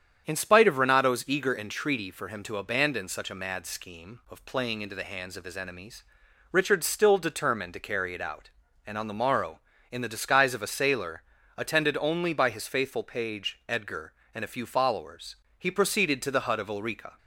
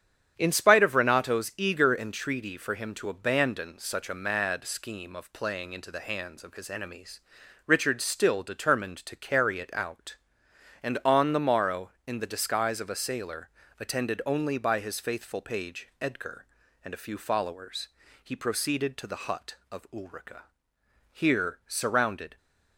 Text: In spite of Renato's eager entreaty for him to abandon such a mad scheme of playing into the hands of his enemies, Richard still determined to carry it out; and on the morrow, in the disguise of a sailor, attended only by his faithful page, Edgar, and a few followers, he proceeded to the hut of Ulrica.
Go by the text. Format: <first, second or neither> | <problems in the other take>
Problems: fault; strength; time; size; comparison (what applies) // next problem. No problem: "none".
first | starts louder than the rest; strong; until 1.3 s; 9 dB; strong in the first // goes on to say "Here surrounded"; noticeable; from 21.1 s on; 1.2 s long